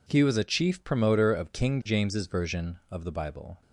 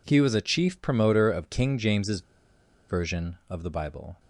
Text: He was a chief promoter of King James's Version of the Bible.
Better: first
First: none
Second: pauses between "James's" and "Version"; noticeable; at 2.2 s; 0.67 s long

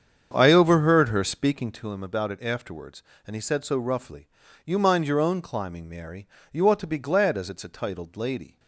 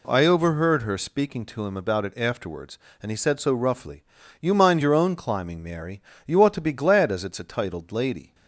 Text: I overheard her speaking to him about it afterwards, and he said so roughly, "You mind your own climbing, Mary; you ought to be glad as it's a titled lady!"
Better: second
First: starts louder than the rest; strong; until 1.9 s; 7.5 dB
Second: none

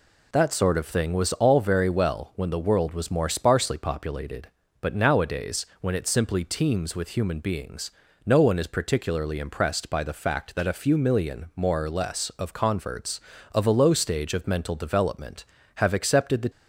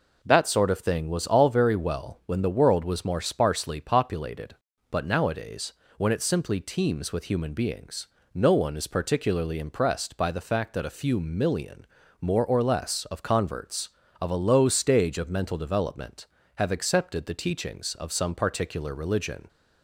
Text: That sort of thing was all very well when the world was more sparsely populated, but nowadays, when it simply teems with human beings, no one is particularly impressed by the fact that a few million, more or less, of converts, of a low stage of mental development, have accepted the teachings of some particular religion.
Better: second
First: stops before "teachings of some particular religion"; at 16.4 s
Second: none

